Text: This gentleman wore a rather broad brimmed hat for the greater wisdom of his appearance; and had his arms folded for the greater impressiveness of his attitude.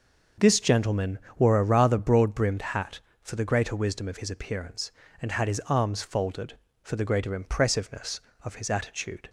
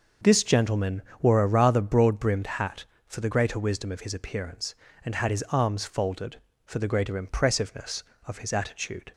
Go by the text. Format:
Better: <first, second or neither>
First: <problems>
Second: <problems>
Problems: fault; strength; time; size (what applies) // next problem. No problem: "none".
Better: neither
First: starts louder than the rest; noticeable; until 1.5 s; 6 dB // pauses between "gentleman" and "wore"; slight; at 1.1 s; 0.18 s long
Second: starts louder than the rest; noticeable; until 1.4 s; 6 dB // pauses between "gentleman" and "wore"; slight; at 1.0 s; 0.18 s long